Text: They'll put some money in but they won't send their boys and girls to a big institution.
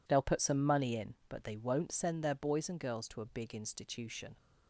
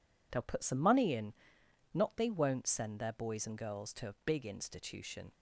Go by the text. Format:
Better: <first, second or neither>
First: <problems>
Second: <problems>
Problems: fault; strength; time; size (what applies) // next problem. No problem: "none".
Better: first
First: none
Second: says "not" for "but"; at 1.9 s